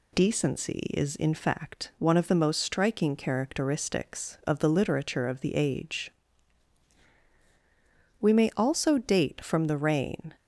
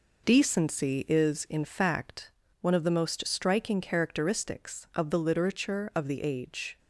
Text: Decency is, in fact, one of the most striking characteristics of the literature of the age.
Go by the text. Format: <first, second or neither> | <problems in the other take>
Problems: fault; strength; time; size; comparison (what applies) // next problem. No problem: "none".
second | goes on to say "We may also date from the reign"; strong; from 8.1 s on; 2.1 s long